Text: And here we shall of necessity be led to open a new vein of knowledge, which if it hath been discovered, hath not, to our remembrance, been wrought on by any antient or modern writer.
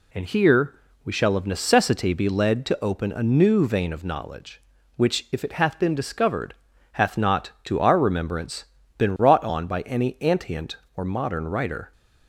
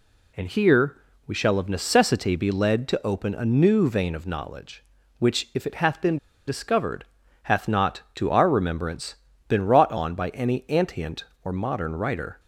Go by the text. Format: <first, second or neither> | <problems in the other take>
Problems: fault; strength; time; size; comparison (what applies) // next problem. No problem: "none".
first | pauses between "here" and "we"; slight; at 0.9 s; 0.30 s long; slight in the first // pauses between "been" and "discovered"; slight; at 6.1 s; 0.30 s long